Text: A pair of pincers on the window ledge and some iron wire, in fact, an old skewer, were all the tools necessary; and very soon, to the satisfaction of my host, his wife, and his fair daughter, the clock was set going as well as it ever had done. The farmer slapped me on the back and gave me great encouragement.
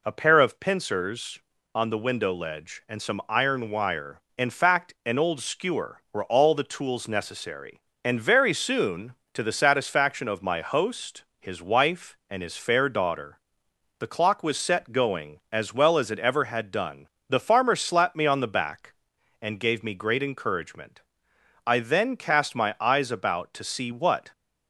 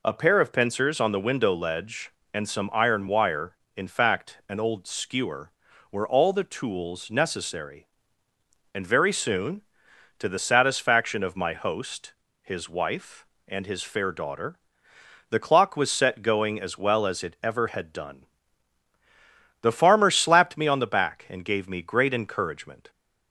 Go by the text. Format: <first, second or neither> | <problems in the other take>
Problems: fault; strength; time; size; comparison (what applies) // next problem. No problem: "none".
second | goes on to say "I then cast my eyes about to see what"; strong; from 21.6 s on; 2.6 s long